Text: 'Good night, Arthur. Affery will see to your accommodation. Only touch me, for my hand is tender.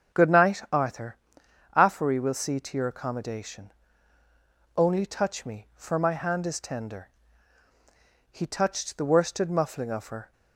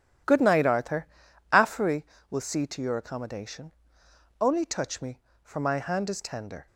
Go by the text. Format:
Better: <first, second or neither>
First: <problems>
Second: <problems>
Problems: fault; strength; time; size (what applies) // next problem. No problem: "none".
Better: second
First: starts louder than the rest; strong; until 1.8 s; 7.5 dB // goes on to say "He touched the worsted muffling of her"; strong; from 8.2 s on; 2.0 s long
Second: none